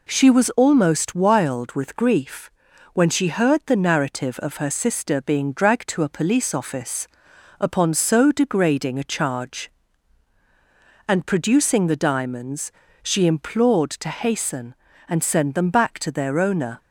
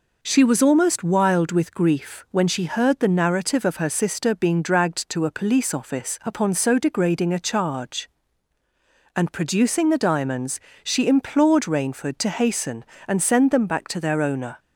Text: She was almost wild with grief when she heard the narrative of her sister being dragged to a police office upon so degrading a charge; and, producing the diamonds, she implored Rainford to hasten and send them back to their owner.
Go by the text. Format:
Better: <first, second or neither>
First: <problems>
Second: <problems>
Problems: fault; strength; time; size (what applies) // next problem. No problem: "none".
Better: second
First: pauses between "grief" and "when"; noticeable; at 2.4 s; 0.46 s long // pauses between "office" and "upon"; noticeable; at 7.0 s; 0.50 s long // skips "Rainford"; at 13.9 s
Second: none